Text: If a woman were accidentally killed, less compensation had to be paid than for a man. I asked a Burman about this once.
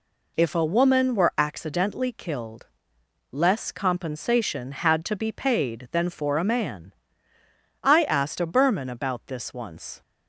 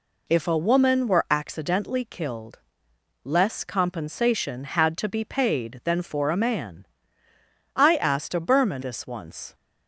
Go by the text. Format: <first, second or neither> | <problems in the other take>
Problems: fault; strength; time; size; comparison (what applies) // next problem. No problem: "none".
first | skips "about"; at 8.8 s